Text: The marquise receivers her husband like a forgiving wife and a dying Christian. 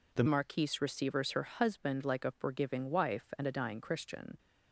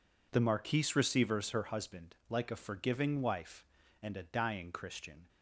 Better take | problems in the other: second | changes voice at "marquise"; from 0.2 s on; 4.1 s long

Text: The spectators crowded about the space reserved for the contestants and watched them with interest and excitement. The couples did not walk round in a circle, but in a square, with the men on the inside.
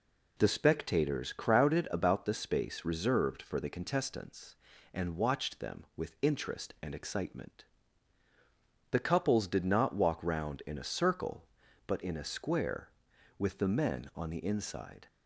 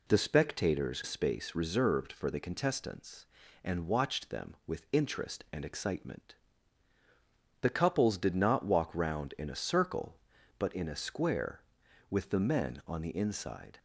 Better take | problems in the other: first | skips "crowded about the"; at 1.0 s

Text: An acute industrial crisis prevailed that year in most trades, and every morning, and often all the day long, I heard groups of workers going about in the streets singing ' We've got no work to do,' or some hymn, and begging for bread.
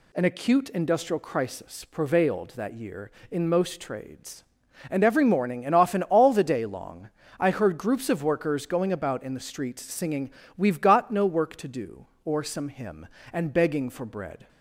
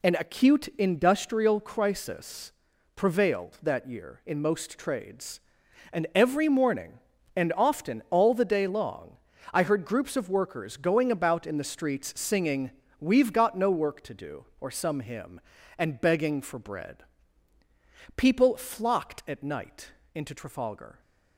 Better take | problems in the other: first | pauses between "crisis" and "prevailed"; at 2.5 s; 0.42 s long // goes on to say "People flocked at night into Trafalgar"; strong; from 18.1 s on; 2.8 s long

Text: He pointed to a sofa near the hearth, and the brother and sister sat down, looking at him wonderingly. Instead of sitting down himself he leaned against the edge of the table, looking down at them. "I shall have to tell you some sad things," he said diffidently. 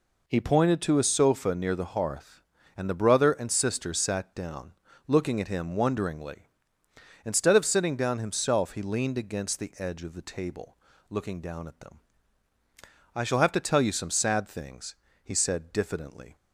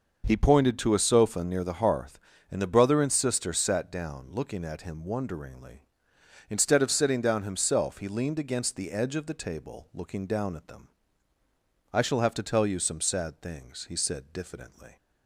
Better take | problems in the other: neither | none

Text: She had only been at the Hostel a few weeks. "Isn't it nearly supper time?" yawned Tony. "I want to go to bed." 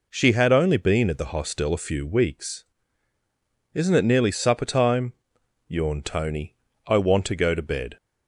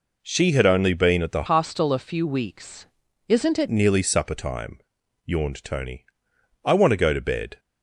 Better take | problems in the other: first | changes voice from "Hostel" to "it"; from 1.4 to 3.6 s; 2.2 s long

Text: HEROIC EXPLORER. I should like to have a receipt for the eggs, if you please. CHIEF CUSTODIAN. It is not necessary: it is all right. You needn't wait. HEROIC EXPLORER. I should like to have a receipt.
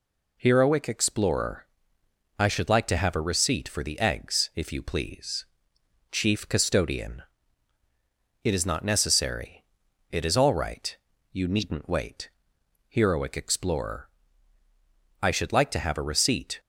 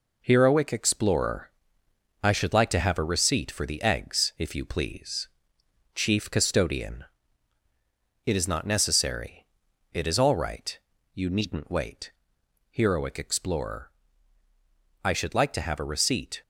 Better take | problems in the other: first | gets quieter; noticeable; throughout; 5.5 dB

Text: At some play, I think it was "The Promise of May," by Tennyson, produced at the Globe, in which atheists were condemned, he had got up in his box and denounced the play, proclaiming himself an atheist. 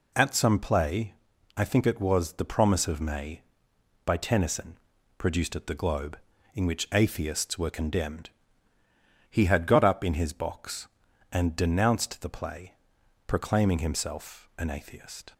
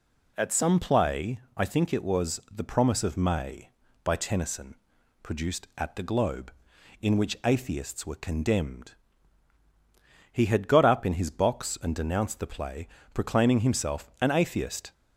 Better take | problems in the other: neither | none

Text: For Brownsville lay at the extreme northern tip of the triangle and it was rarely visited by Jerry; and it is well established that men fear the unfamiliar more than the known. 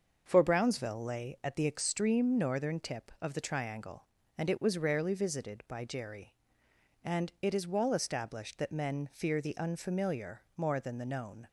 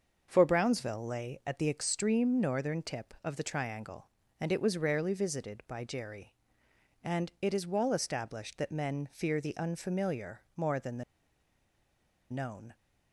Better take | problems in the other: first | starts louder than the rest; until 1.3 s; 6.5 dB; also in the first // pauses between "the" and "known"; strong; at 11.0 s; 1.2 s long

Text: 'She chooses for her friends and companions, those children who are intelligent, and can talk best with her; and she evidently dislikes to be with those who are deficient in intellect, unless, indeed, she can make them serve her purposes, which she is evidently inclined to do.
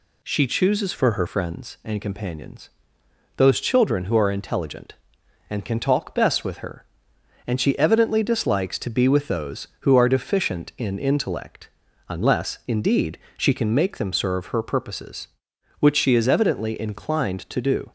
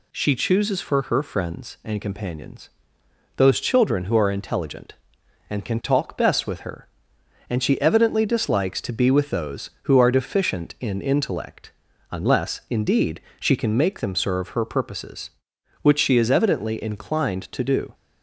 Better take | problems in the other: second | changes voice from "for" to "her"; from 0.9 to 1.2 s; 0.3 s long

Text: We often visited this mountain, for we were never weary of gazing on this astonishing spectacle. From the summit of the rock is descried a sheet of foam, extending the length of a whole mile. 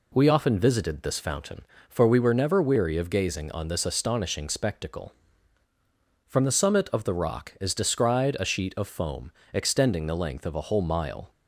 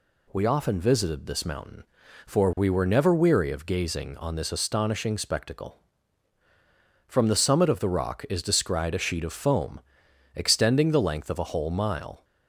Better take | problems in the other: second | says "fountain" for "mountain"; at 1.2 s

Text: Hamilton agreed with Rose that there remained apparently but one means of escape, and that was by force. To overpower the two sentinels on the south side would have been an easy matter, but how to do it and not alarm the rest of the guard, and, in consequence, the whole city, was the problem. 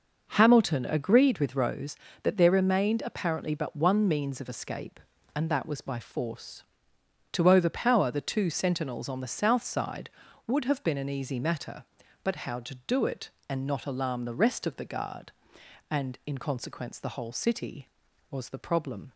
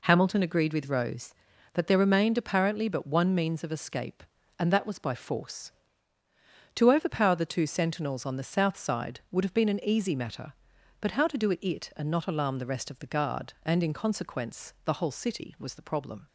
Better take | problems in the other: first | says "it" twice; at 11.6 s

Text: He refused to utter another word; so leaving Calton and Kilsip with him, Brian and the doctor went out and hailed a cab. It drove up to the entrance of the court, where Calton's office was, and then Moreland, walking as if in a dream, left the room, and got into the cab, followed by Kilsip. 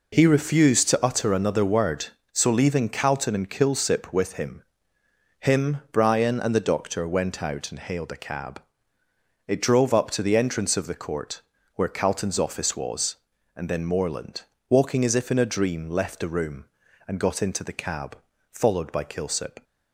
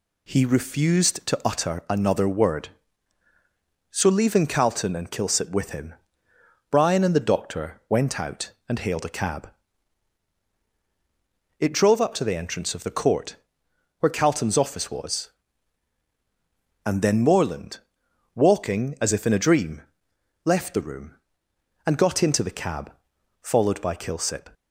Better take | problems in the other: second | says "him" twice; at 5.3 s

